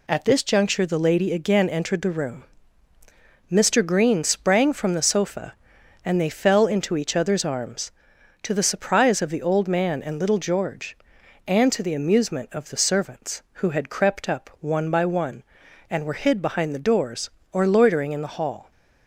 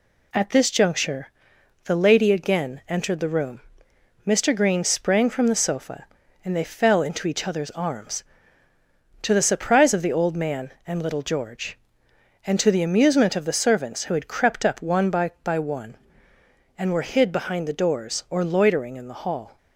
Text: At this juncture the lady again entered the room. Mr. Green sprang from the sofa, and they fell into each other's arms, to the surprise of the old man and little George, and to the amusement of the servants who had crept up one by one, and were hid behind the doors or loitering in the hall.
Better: first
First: none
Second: pauses between "juncture" and "the"; noticeable; at 1.2 s; 0.58 s long // says "by" twice; at 15.4 s

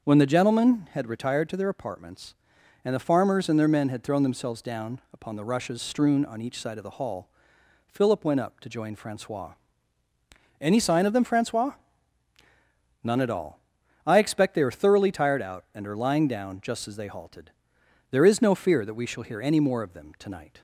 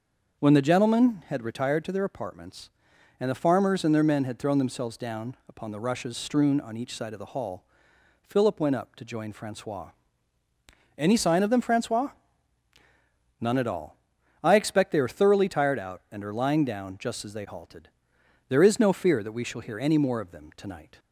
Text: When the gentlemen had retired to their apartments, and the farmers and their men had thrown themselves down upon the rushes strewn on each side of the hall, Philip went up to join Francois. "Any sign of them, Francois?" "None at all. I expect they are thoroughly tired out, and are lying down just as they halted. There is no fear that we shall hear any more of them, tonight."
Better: neither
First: starts louder than the rest; until 1.0 s; 6.5 dB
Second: starts louder than the rest; until 1.4 s; 6.5 dB

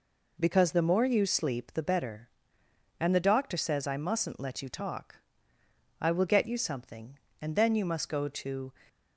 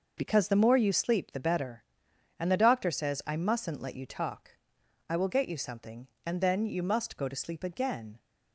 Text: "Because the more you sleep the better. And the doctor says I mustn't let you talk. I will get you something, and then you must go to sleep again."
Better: second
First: stops before "sleep again"; at 8.8 s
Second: none

